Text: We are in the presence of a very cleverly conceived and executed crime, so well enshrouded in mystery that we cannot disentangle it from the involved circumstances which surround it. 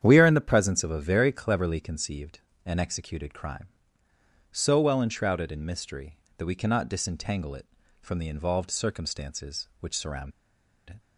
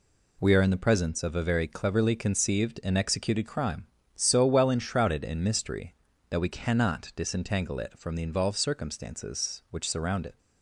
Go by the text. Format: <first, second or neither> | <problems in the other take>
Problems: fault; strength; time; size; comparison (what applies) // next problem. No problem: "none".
second | starts louder than the rest; strong; until 1.0 s; 9 dB // pauses between "surround" and "it"; noticeable; at 10.3 s; 0.58 s long